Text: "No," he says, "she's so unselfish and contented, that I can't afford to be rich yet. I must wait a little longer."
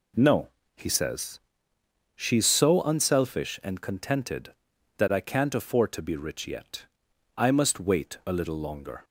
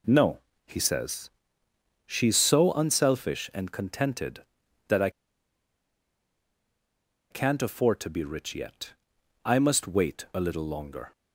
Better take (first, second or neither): first